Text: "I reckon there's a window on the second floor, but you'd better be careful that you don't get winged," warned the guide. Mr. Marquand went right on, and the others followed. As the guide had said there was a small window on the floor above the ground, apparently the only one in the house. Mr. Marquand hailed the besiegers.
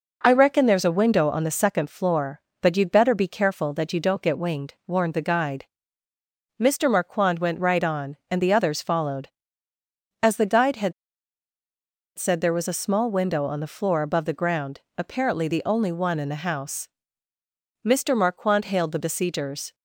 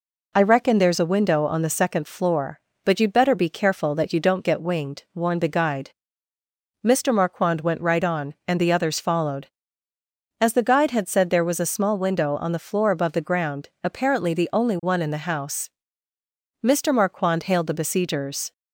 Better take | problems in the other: second | pauses between "had" and "said"; strong; at 10.9 s; 1.2 s long

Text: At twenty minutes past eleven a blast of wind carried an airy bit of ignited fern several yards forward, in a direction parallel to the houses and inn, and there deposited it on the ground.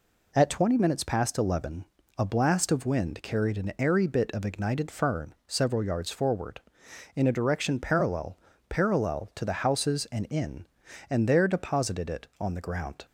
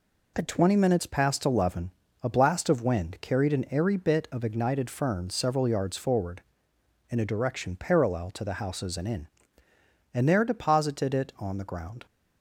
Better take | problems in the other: second | pauses between "eleven" and "a"; slight; at 1.8 s; 0.32 s long; slight in the second // says "parallel" twice; at 8.7 s

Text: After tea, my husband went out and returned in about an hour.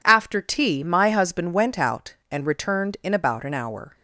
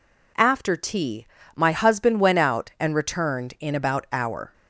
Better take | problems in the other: first | skips "an"; at 4.0 s

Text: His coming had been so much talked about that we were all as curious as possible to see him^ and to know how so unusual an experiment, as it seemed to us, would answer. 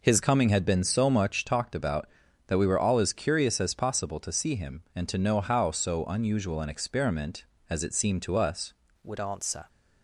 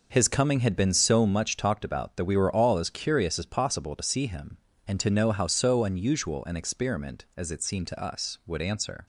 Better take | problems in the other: second | changes voice at "would"; from 9.0 s on; 0.6 s long

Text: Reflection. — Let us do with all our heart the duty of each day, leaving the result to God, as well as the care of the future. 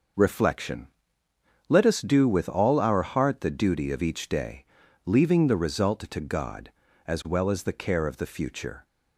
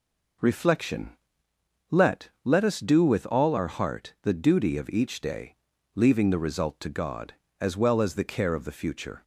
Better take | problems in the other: first | says "Let" twice; at 2.4 s

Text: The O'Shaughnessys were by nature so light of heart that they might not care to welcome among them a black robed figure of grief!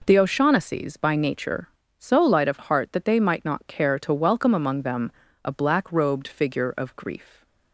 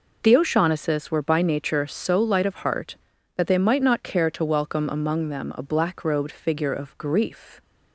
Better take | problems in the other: second | skips "were"; at 0.9 s // pauses between "them" and "a"; slight; at 5.1 s; 0.32 s long

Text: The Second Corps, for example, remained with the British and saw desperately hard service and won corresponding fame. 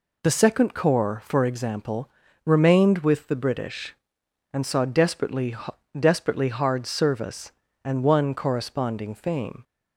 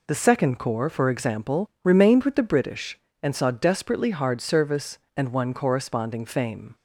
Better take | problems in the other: second | says "desperately" twice; at 5.9 s

